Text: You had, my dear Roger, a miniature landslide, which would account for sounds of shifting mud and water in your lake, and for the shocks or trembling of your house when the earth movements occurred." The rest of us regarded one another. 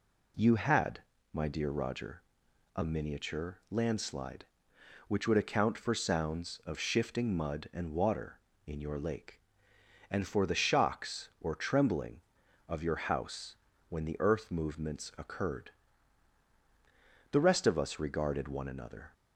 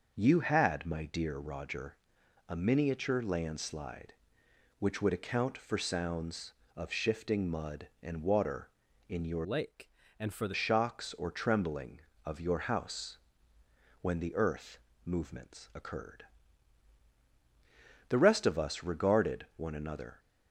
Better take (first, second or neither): first